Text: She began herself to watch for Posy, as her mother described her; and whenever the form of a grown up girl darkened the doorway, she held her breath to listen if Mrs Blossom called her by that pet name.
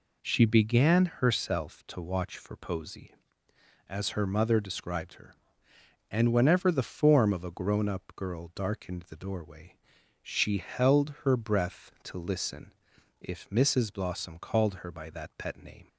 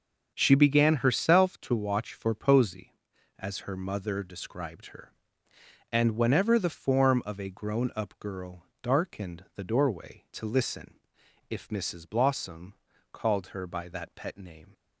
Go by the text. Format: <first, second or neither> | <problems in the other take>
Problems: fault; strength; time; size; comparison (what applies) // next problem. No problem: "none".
first | starts louder than the rest; until 1.3 s; 6.5 dB // pauses between "girl" and "darkened"; slight; at 8.6 s; 0.16 s long // skips "she held her breath"; at 10.2 s // pauses between "listen" and "if"; noticeable; at 10.9 s; 0.56 s long; noticeable in the first // pauses between "Blossom" and "called"; at 12.7 s; 0.40 s long